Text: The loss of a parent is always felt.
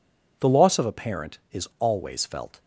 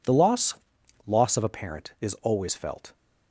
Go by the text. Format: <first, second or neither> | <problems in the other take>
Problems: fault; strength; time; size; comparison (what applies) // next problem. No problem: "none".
first | says "loss" twice; at 1.0 s